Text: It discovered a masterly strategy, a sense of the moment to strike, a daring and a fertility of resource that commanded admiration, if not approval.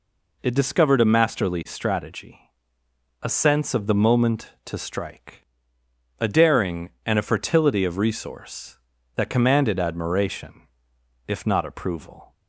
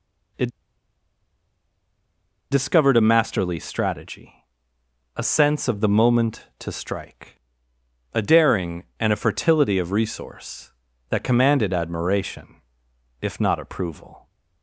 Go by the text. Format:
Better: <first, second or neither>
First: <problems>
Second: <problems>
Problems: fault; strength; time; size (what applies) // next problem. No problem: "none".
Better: first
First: none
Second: pauses between "It" and "discovered"; strong; at 0.4 s; 2.0 s long